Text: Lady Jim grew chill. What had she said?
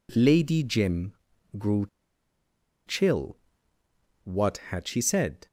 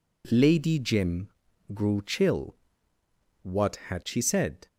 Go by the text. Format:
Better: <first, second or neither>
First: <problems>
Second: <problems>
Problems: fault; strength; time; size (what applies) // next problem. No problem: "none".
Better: second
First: pauses between "Jim" and "grew"; at 1.1 s; 0.44 s long // pauses between "grew" and "chill"; at 1.8 s; 1.0 s long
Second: pauses between "Jim" and "grew"; at 1.2 s; 0.44 s long